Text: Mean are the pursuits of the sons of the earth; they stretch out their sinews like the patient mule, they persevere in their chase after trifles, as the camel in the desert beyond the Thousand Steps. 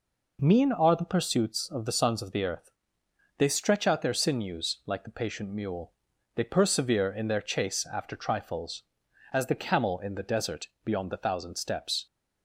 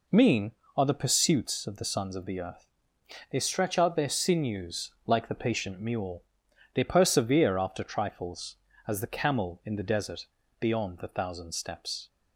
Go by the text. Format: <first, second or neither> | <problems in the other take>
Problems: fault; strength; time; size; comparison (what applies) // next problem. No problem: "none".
first | skips "in their chase"; at 7.5 s // pauses between "desert" and "beyond"; slight; at 10.2 s; 0.36 s long